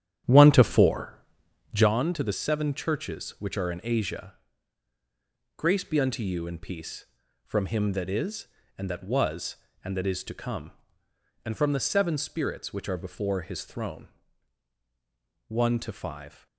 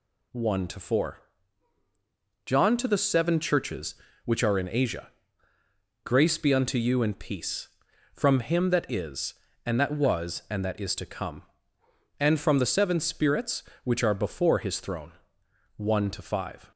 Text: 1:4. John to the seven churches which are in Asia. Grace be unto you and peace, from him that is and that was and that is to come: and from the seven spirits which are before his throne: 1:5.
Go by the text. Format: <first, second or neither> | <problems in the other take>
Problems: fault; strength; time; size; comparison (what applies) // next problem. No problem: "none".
second | starts louder than the rest; strong; until 1.9 s; 10 dB